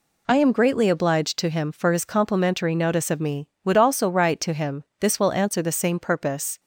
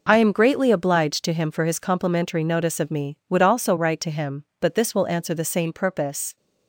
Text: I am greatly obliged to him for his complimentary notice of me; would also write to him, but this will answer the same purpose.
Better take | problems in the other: second | skips "but"; at 4.9 s

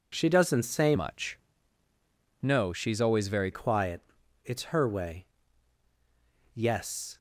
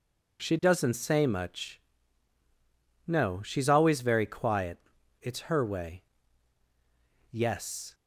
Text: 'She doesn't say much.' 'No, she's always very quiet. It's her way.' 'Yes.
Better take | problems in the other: second | changes voice from "much" to "very"; from 0.9 to 3.4 s; 2.5 s long

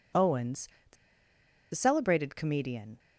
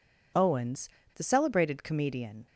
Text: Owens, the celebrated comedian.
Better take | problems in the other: second | pauses between "the" and "celebrated"; noticeable; at 0.9 s; 0.78 s long

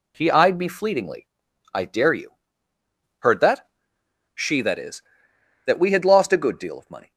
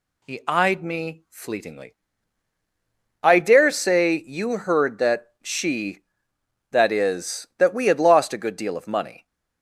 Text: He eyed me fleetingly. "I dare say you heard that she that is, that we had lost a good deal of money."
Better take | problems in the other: second | skips "say"; at 2.1 s // pauses between "you" and "heard"; noticeable; at 2.3 s; 0.84 s long // pauses between "that" and "she"; noticeable; at 3.6 s; 0.64 s long

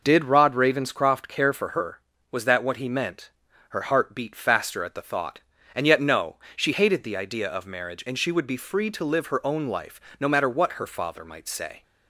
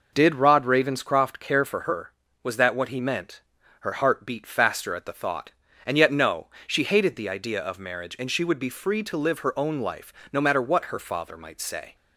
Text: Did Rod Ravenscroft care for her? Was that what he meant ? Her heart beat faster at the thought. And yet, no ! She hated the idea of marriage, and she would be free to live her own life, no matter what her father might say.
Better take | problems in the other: neither | none

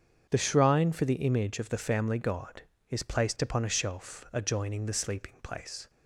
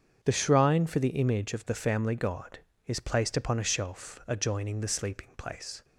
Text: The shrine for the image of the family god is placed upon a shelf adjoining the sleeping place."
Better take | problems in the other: neither | starts louder than the rest; strong; the same in both

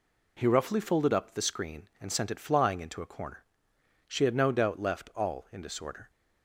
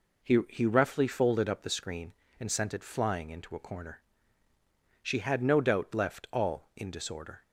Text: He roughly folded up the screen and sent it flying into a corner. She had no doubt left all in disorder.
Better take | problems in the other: first | says "He" twice; at 0.4 s

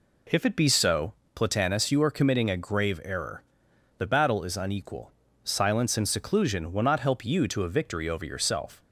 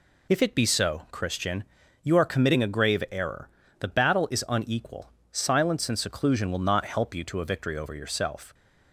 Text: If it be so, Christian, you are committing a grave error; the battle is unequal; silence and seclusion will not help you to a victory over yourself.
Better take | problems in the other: second | says "Platanus" for "Christian"; at 1.3 s

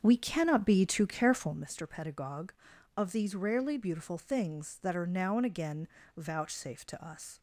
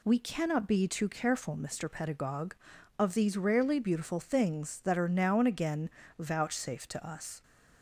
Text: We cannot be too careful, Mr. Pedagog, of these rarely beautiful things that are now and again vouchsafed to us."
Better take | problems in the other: second | starts louder than the rest; strong; until 1.6 s; 7 dB // pauses between "again" and "vouchsafed"; slight; at 5.8 s; 0.30 s long; slight in the second

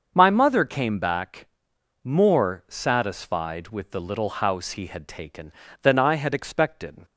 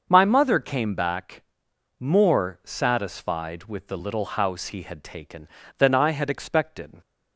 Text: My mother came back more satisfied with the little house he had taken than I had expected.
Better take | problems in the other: neither | starts louder than the rest; the same in both // pauses between "back" and "more"; noticeable; the same in both

